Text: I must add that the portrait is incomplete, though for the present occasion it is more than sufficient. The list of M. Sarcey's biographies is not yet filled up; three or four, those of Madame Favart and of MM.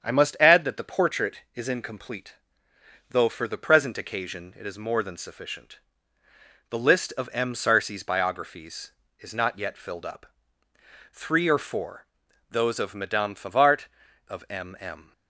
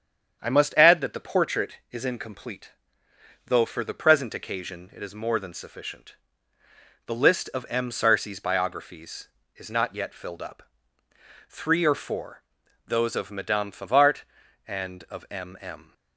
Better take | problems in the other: second | starts louder than the rest; strong; until 1.0 s; 8 dB; strong in the second // skips "and"; at 14.0 s

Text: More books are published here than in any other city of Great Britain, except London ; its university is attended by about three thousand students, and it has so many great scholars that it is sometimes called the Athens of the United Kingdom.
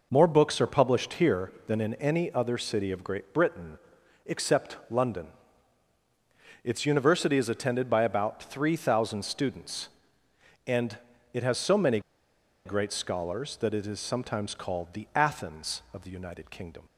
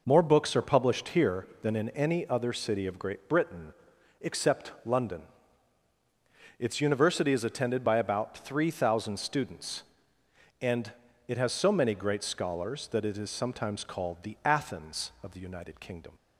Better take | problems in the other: second | pauses between "and" and "it"; slight; at 10.9 s; 0.34 s long; slight in the second // pauses between "many" and "great"; noticeable; at 11.9 s; 0.66 s long

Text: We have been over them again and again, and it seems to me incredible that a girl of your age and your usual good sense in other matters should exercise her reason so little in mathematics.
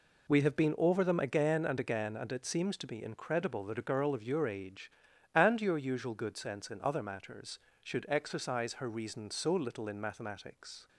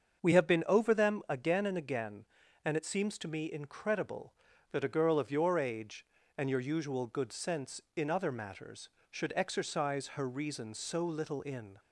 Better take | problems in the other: first | starts louder than the rest; until 1.3 s; 7 dB // stops before "mathematics"; at 11.7 s

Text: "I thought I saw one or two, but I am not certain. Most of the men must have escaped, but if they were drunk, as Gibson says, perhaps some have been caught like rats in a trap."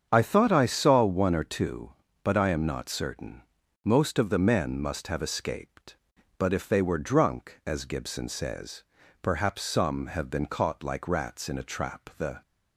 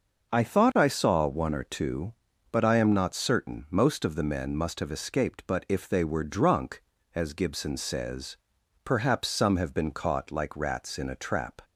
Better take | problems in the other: second | starts louder than the rest; strong; until 1.1 s; 8 dB; noticeable in the second // goes on to say "The"; slight; from 12.1 s on; 0.22 s long

